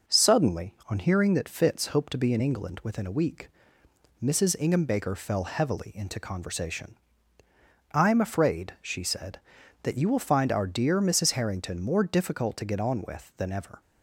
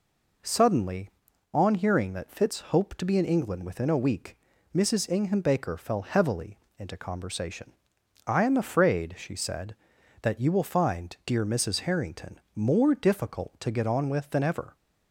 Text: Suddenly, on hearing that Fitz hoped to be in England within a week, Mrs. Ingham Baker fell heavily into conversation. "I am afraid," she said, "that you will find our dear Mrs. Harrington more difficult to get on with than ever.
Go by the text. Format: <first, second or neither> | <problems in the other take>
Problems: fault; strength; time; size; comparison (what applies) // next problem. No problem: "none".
first | pauses between "heavily" and "into"; slight; at 6.5 s; 0.19 s long // skips "our"; at 11.2 s // pauses between "Harrington" and "more"; slight; at 12.3 s; 0.16 s long